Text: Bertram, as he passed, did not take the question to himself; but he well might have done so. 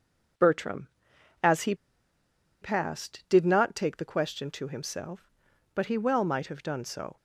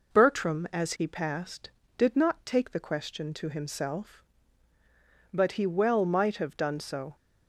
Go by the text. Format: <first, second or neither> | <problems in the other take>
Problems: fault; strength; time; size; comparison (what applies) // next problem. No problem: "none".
second | pauses between "he" and "passed"; noticeable; at 1.7 s; 0.87 s long